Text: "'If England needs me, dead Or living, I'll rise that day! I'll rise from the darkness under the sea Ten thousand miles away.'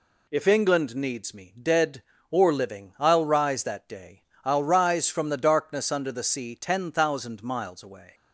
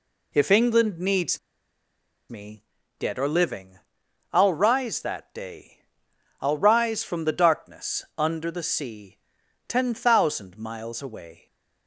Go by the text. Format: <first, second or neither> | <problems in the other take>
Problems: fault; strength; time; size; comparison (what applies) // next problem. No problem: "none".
first | pauses between "needs" and "me"; noticeable; at 1.3 s; 0.91 s long // pauses between "sea" and "Ten"; noticeable; at 9.1 s; 0.50 s long